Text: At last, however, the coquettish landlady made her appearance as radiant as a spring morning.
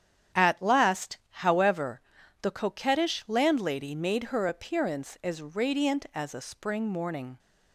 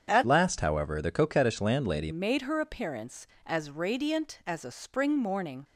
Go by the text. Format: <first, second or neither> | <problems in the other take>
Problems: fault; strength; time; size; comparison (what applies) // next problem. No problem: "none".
first | starts louder than the rest; strong; until 1.1 s; 7.5 dB; strong in the first // changes voice from "last" to "landlady"; from 0.2 to 2.1 s; 1.9 s long